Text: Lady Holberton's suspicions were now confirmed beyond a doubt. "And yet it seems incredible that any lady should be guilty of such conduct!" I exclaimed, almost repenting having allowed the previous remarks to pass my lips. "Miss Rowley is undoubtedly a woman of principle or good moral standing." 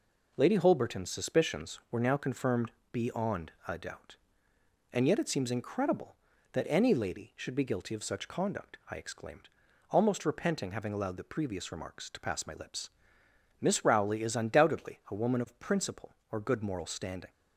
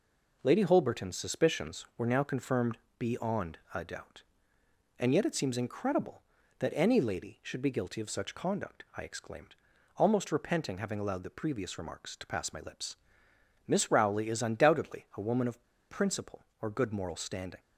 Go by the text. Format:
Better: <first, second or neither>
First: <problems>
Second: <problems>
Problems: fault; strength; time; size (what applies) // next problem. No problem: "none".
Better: first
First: pauses between "confirmed" and "beyond"; slight; at 2.7 s; 0.20 s long // pauses between "beyond" and "a"; slight; at 3.5 s; 0.16 s long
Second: pauses between "confirmed" and "beyond"; slight; at 2.7 s; 0.20 s long // pauses between "beyond" and "a"; slight; at 3.5 s; 0.16 s long // pauses between "of" and "principle"; slight; at 15.6 s; 0.26 s long